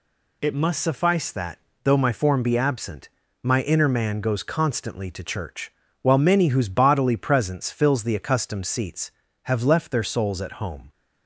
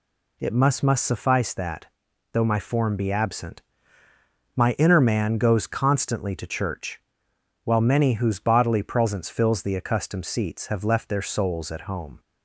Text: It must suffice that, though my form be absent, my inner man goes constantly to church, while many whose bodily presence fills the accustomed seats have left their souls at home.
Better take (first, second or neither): first